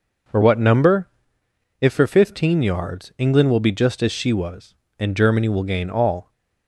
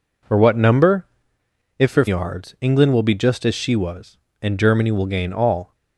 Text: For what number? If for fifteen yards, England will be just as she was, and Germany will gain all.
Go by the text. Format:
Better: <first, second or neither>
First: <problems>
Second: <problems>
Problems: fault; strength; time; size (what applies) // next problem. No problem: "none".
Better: first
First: none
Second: skips "fifteen"; at 2.0 s